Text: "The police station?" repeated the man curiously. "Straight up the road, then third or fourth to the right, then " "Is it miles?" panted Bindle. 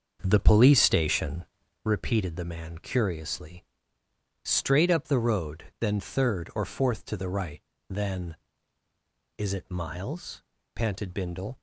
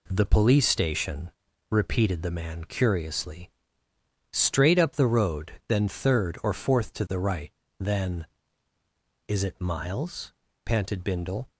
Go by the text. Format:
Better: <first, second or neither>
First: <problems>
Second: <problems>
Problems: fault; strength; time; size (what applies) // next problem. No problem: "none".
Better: second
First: starts louder than the rest; until 1.9 s; 6.5 dB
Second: none